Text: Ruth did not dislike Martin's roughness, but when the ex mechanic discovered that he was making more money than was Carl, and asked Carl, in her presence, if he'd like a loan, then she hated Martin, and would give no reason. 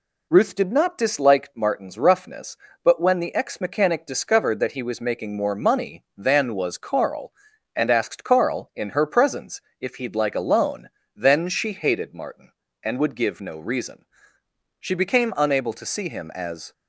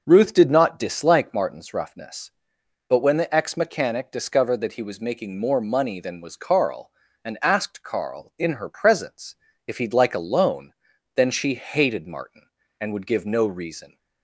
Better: second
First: goes on to say "She became unable to see him as"; strong; from 14.7 s on; 1.9 s long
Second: none

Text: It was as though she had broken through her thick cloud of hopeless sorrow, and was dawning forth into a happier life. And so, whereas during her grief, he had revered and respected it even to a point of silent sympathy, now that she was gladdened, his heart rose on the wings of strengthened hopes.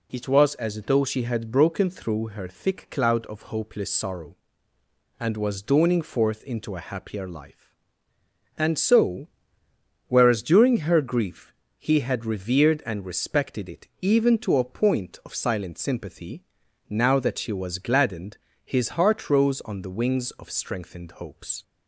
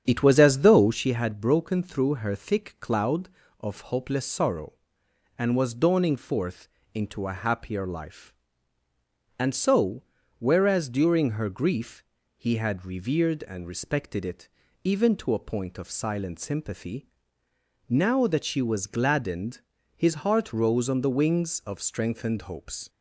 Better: first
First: none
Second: starts louder than the rest; strong; until 1.1 s; 8 dB // pauses between "forth" and "into"; slight; at 6.6 s; 0.26 s long // pauses between "it" and "even"; slight; at 14.4 s; 0.36 s long

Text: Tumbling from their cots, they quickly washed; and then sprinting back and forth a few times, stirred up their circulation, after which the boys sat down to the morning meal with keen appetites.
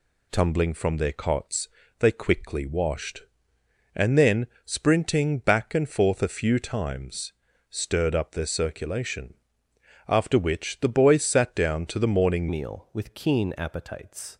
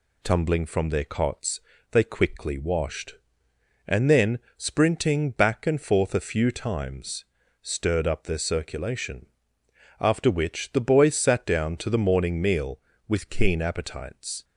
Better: second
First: pauses between "then" and "sprinting"; slight; at 4.4 s; 0.20 s long // changes voice at "meal"; from 12.4 s on; 1.9 s long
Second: pauses between "then" and "sprinting"; slight; at 4.3 s; 0.20 s long

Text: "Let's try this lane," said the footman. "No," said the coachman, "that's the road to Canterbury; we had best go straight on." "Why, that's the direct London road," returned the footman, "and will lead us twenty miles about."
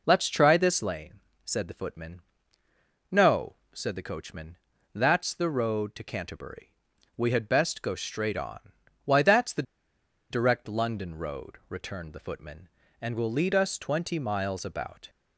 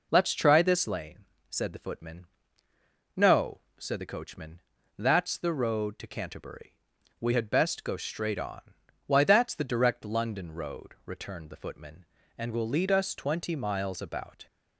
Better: second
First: pauses between "the" and "direct"; noticeable; at 9.6 s; 0.68 s long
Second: none

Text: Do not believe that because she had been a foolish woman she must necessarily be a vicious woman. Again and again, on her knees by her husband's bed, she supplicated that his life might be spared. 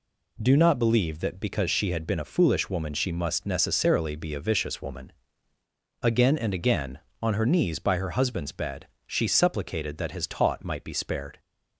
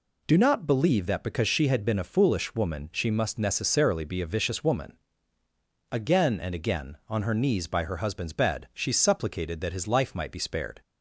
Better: second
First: says "taut" for "life"; at 10.2 s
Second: none

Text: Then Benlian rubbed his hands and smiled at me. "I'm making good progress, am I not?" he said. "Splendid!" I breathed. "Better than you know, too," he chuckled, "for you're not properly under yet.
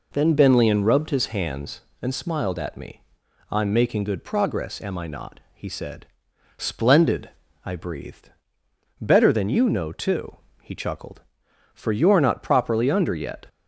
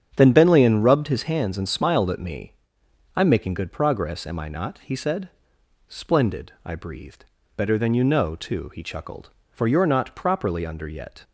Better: first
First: none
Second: starts louder than the rest; strong; until 1.3 s; 8 dB

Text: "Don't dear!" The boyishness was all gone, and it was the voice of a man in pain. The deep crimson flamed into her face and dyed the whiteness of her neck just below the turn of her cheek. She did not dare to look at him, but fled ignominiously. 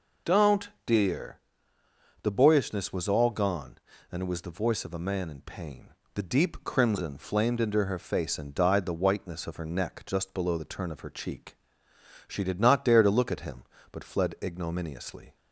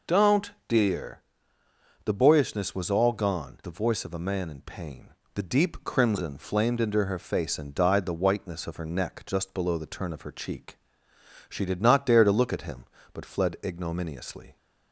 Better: first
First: pauses between "Don't" and "dear"; slight; at 0.6 s; 0.16 s long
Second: pauses between "Don't" and "dear"; slight; at 0.5 s; 0.16 s long // skips "and it was"; at 3.6 s

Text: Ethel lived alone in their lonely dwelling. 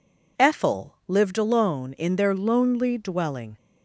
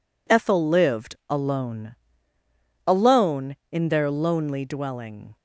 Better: first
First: none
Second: says "alone" twice; at 2.8 s

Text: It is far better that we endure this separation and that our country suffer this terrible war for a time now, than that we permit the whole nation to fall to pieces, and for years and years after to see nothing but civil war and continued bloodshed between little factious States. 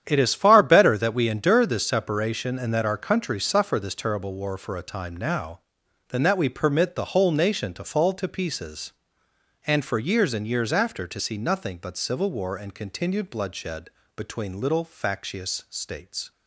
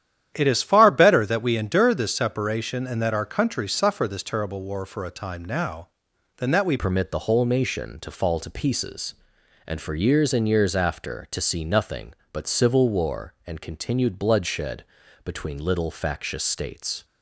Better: first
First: starts louder than the rest; strong; until 1.0 s; 9.5 dB // pauses between "bloodshed" and "between"; slight; at 13.8 s; 0.28 s long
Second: starts louder than the rest; strong; until 1.3 s; 10.5 dB // changes voice at "permit"; from 6.7 s on; 10.3 s long // pauses between "bloodshed" and "between"; at 14.8 s; 0.40 s long

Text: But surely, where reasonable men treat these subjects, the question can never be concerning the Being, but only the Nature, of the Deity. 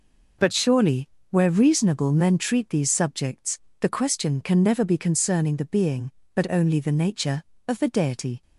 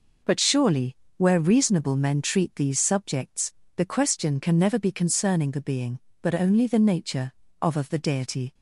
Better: first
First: none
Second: says "of" twice; at 7.7 s

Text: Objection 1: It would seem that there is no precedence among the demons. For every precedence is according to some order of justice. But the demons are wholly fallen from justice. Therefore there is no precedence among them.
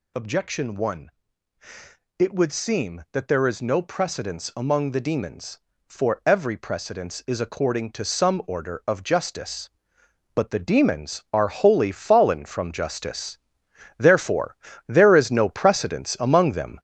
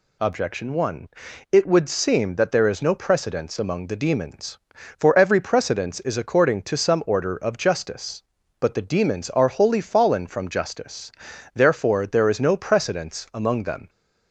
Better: second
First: gets louder; throughout; 6 dB // pauses between "Therefore" and "there"; slight; at 14.5 s; 0.32 s long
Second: none

